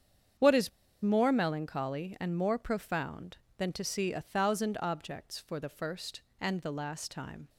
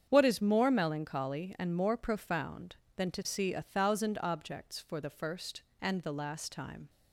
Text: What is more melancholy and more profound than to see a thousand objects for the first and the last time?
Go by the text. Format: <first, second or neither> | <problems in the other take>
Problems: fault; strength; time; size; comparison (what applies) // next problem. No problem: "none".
second | starts louder than the rest; strong; until 1.7 s; 8 dB; strong in the second // pauses between "is" and "more"; slight; at 0.6 s; 0.32 s long